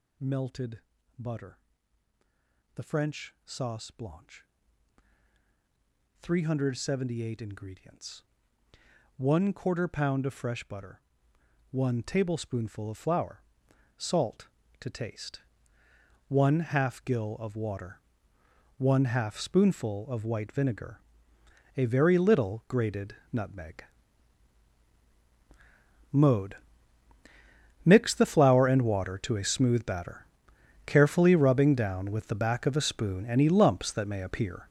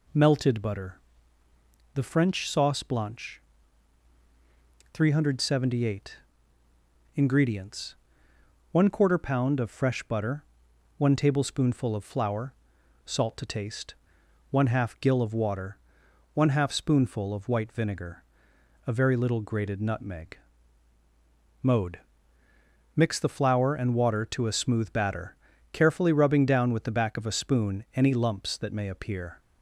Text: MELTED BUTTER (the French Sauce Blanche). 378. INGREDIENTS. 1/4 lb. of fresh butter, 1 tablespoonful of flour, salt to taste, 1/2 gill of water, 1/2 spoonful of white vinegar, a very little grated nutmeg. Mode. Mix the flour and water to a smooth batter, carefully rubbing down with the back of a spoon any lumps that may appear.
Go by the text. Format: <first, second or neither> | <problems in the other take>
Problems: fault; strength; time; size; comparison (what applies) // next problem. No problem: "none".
second | gets louder; strong; throughout; 11.5 dB // pauses between "MELTED" and "BUTTER"; slight; at 0.8 s; 0.36 s long // pauses between "grated" and "nutmeg"; slight; at 23.1 s; 0.18 s long